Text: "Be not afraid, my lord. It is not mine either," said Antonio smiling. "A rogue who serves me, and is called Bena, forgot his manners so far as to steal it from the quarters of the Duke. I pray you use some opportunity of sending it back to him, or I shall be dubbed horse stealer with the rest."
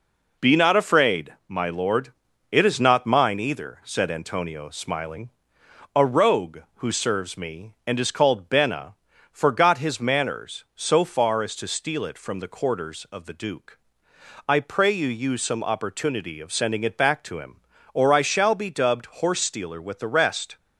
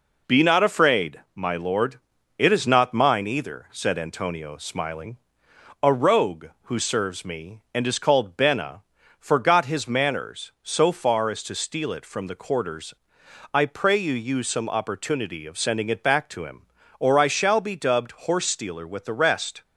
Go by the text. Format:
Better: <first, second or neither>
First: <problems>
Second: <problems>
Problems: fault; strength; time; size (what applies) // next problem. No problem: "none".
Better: first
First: none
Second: skips "of the Duke"; at 13.2 s